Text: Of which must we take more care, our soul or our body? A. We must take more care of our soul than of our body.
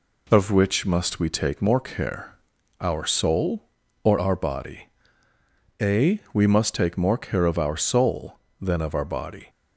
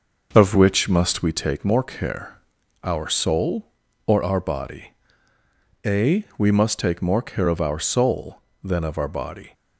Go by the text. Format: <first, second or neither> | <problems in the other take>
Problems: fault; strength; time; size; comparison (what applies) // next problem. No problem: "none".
first | starts louder than the rest; noticeable; until 1.3 s; 6 dB